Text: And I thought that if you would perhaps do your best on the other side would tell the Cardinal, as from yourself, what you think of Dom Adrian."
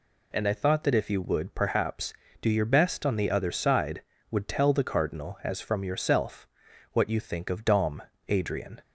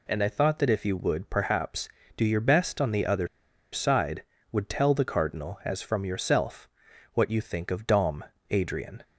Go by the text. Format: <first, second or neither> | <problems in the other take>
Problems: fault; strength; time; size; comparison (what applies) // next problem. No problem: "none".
first | pauses between "other" and "side"; at 3.2 s; 0.45 s long // pauses between "Dom" and "Adrian"; slight; at 8.2 s; 0.28 s long; slight in the first